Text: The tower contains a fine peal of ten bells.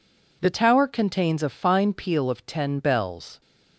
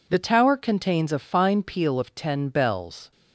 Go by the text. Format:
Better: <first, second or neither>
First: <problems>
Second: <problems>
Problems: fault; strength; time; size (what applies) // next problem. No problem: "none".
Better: neither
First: none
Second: none